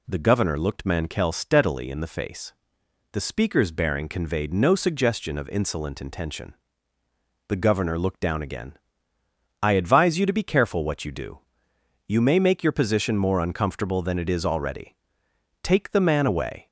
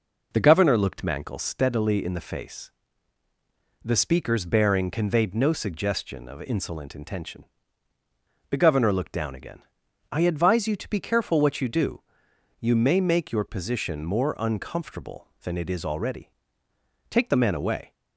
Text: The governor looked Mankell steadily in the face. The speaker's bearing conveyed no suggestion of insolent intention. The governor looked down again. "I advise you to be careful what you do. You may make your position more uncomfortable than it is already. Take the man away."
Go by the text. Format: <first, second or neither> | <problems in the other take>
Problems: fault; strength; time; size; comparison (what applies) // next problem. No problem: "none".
neither | none